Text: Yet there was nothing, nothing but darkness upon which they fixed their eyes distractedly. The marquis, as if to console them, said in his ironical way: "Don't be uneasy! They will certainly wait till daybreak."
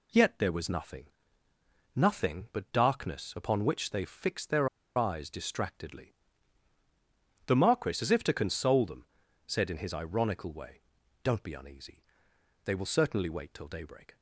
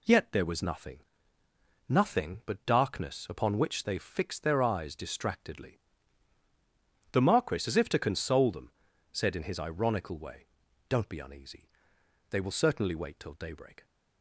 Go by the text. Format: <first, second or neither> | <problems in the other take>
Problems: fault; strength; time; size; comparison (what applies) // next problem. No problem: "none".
second | pauses between "their" and "eyes"; slight; at 4.6 s; 0.29 s long